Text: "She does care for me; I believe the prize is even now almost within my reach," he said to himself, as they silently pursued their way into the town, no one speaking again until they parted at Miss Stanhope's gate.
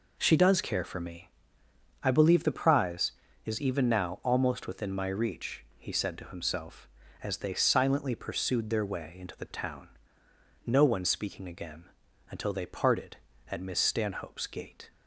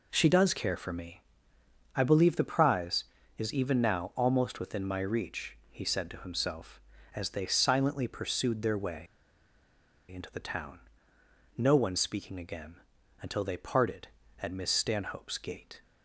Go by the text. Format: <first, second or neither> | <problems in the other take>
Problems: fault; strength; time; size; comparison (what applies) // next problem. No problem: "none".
first | pauses between "way" and "into"; at 9.0 s; 1.0 s long // pauses between "again" and "until"; at 12.7 s; 0.44 s long; also in the first